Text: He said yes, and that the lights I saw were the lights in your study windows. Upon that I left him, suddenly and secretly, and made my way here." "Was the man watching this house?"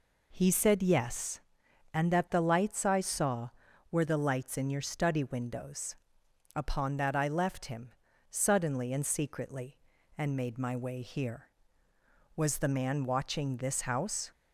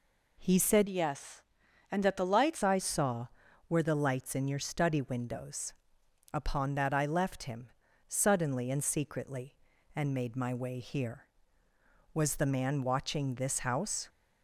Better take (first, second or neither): first